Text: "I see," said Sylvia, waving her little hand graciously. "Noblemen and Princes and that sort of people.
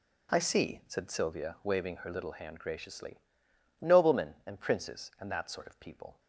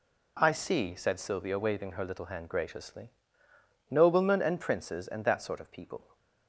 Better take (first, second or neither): neither